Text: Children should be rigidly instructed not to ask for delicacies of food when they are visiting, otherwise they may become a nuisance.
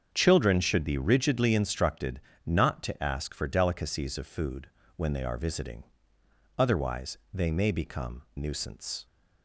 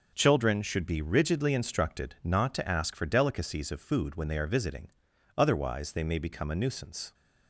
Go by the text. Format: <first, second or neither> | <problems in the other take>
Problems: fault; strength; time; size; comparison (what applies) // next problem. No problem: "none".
second | starts louder than the rest; strong; until 1.1 s; 7 dB // pauses between "instructed" and "not"; slight; at 2.1 s; 0.26 s long // pauses between "food" and "when"; slight; at 4.6 s; 0.30 s long // pauses between "otherwise" and "they"; slight; at 7.1 s; 0.16 s long // skips "a"; at 8.2 s